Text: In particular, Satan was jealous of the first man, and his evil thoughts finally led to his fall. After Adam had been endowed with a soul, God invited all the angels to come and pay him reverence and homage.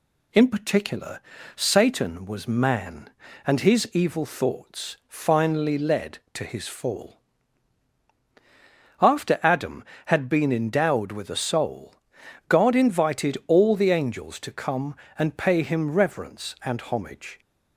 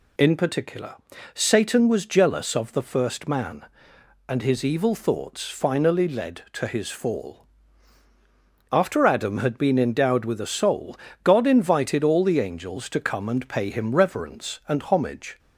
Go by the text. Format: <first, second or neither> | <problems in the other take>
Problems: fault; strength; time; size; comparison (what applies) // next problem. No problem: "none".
second | skips "jealous of the first"; at 2.4 s